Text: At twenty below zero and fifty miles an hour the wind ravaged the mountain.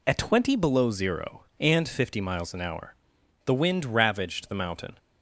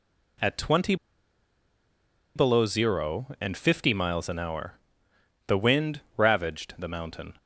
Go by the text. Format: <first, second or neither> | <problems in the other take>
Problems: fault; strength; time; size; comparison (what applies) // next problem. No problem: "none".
first | pauses between "twenty" and "below"; strong; at 0.9 s; 1.4 s long // pauses between "hour" and "the"; noticeable; at 4.7 s; 0.72 s long; noticeable in the first // pauses between "wind" and "ravaged"; slight; at 6.0 s; 0.16 s long